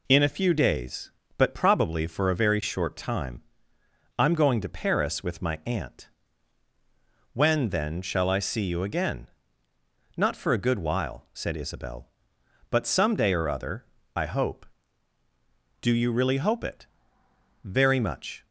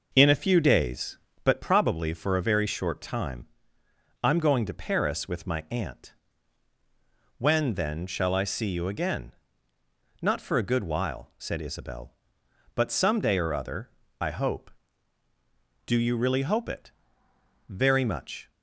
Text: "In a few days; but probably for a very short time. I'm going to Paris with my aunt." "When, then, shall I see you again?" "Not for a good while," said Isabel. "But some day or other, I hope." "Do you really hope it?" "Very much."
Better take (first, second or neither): first